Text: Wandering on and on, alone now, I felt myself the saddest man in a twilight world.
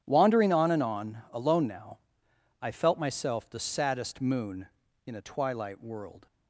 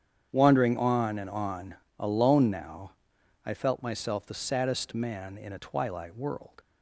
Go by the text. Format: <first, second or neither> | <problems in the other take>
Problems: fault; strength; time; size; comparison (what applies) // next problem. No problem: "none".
second | starts louder than the rest; strong; until 1.0 s; 9.5 dB; strong in the second // says "moon" for "man"; at 4.2 s